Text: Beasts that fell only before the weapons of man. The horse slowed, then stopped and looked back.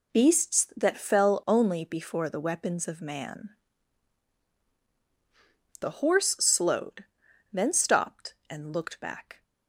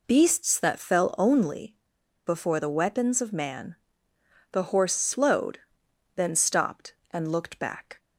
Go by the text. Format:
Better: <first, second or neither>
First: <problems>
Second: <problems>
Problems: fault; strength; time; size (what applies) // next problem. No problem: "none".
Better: first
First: none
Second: pauses between "only" and "before"; noticeable; at 1.7 s; 0.48 s long